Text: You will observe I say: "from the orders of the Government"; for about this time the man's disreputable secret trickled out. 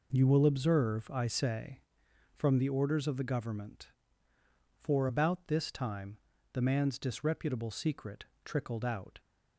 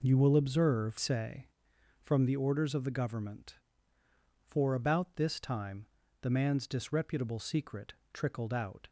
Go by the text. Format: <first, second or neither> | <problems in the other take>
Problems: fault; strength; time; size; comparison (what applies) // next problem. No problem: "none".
first | skips "I"; at 0.9 s // pauses between "time" and "the"; slight; at 5.8 s; 0.36 s long; slight in the first // pauses between "secret" and "trickled"; slight; at 7.9 s; 0.20 s long; slight in the first